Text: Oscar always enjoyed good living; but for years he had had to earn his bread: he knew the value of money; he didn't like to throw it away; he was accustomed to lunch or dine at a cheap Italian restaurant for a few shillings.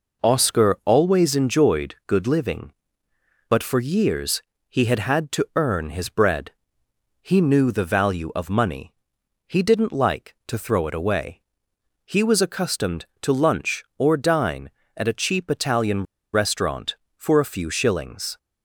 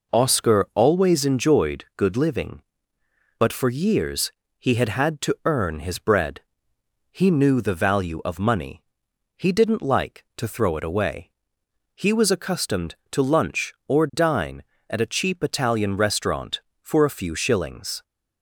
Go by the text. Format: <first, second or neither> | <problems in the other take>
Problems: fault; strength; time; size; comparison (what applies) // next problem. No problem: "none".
second | pauses between "years" and "he"; slight; at 4.4 s; 0.26 s long; slight in the second // pauses between "Italian" and "restaurant"; slight; at 16.0 s; 0.30 s long